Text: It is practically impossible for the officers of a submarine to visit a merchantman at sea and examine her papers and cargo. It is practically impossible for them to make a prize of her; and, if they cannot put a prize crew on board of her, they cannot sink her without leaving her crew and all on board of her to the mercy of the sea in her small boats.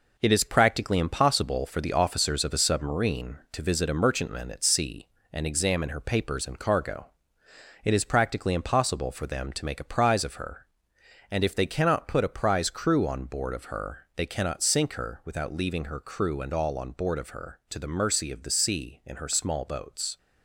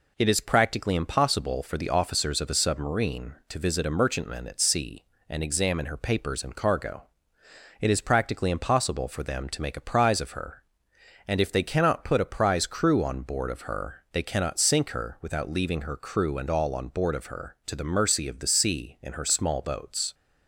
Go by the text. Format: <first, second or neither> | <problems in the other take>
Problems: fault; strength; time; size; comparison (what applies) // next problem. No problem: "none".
second | gets quieter; throughout; 6 dB